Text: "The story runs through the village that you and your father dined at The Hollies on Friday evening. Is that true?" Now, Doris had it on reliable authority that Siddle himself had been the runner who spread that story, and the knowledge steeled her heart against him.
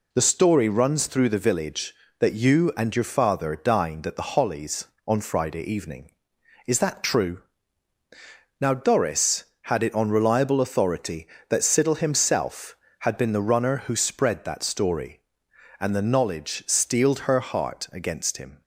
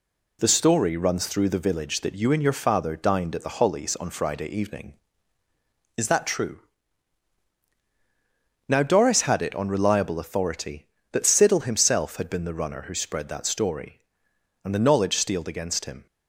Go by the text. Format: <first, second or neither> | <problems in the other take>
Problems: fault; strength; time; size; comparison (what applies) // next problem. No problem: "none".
first | skips "her heart"; at 15.4 s